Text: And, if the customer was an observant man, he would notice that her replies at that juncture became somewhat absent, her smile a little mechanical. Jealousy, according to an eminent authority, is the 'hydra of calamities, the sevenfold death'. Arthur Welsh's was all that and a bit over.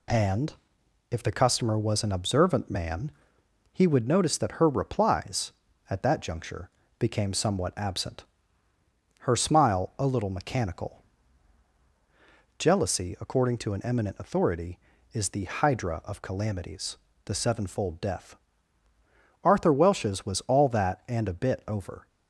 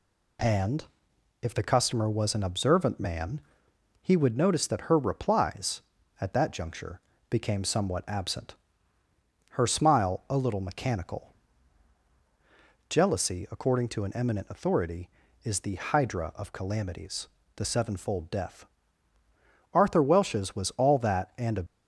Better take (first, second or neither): first